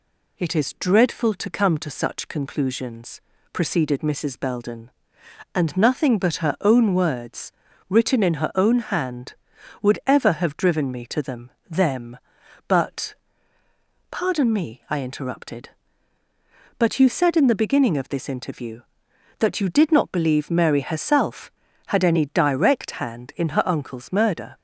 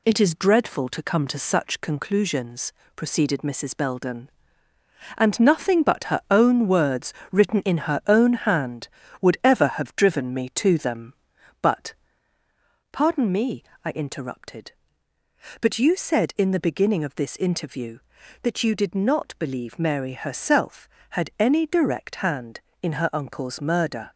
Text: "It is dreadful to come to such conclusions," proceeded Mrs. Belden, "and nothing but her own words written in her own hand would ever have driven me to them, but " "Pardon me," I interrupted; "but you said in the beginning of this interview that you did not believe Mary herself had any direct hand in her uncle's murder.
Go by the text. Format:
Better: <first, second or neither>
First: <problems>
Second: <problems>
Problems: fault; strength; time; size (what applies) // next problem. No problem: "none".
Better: second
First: pauses between "words" and "written"; slight; at 7.5 s; 0.36 s long // says "them" twice; at 11.6 s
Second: pauses between "words" and "written"; slight; at 7.1 s; 0.16 s long